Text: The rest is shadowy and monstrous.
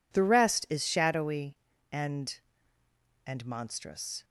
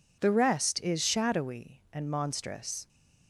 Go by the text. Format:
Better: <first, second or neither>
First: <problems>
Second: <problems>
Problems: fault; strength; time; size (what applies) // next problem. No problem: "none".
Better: second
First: says "and" twice; at 3.2 s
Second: none